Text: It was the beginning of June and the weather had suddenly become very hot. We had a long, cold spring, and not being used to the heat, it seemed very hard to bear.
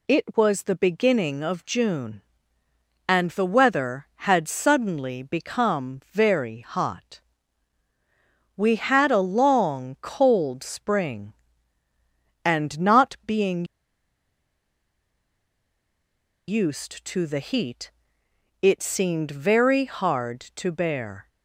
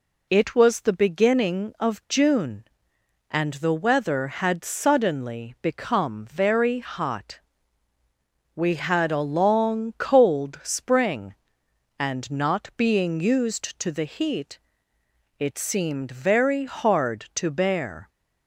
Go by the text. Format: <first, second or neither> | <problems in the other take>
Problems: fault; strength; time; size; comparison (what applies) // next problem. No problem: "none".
second | pauses between "being" and "used"; strong; at 13.6 s; 2.8 s long